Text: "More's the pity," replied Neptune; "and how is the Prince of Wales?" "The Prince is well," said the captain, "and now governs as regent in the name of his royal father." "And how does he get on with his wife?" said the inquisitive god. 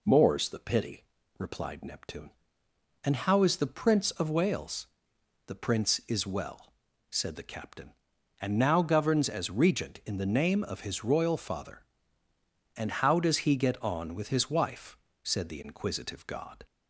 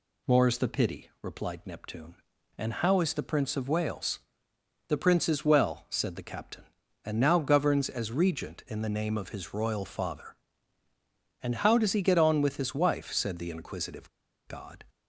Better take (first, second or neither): first